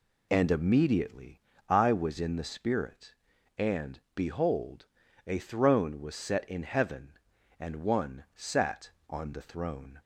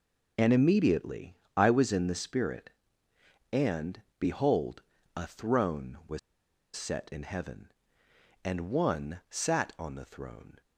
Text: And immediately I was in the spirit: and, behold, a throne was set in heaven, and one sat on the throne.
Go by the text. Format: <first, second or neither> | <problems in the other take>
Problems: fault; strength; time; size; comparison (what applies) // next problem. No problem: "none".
first | pauses between "immediately" and "I"; slight; at 1.3 s; 0.22 s long; slight in the first // pauses between "was" and "set"; noticeable; at 6.1 s; 0.56 s long